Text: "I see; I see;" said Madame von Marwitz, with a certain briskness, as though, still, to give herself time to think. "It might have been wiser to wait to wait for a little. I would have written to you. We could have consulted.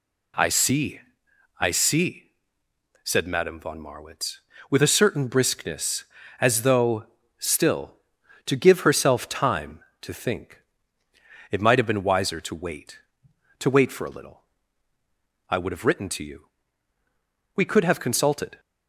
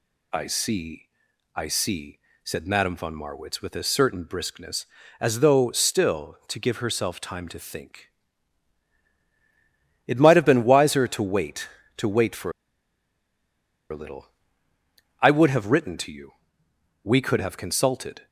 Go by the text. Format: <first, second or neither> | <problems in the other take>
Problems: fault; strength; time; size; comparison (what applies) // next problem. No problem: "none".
first | pauses between "for" and "a"; strong; at 12.5 s; 1.3 s long